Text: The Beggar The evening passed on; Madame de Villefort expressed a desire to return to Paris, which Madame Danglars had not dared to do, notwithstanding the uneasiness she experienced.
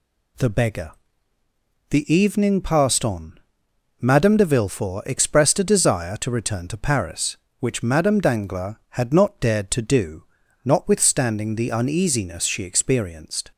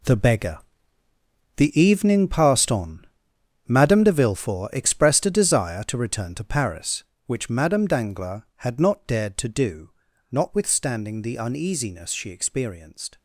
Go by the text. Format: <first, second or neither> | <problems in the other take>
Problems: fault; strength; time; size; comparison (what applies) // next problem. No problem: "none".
first | gets quieter; strong; throughout; 12.5 dB // pauses between "Beggar" and "The"; at 0.5 s; 1.0 s long; also in the first